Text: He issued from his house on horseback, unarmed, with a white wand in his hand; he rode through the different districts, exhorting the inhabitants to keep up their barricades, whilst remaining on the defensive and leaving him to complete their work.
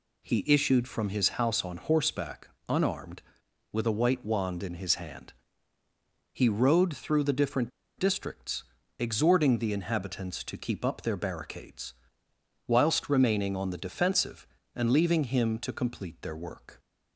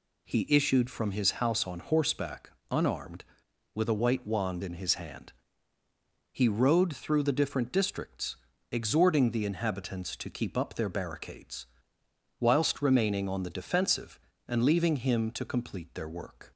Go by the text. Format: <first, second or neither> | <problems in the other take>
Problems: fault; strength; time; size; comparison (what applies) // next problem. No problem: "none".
second | pauses between "different" and "districts"; slight; at 7.7 s; 0.28 s long